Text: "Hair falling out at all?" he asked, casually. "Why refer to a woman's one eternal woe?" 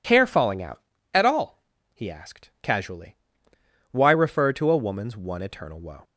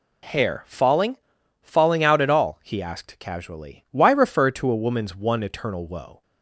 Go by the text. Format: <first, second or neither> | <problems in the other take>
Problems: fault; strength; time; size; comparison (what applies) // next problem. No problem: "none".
first | says "falling" twice; at 1.6 s